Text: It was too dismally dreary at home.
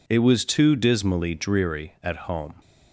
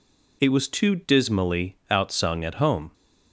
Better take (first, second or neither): first